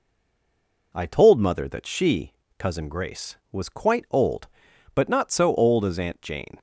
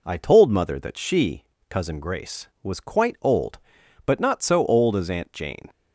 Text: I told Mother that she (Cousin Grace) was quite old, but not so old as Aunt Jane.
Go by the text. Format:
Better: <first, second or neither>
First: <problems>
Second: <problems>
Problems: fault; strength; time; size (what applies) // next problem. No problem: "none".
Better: second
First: stays silent before the first word; slight; until 0.9 s; 0.9 s long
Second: none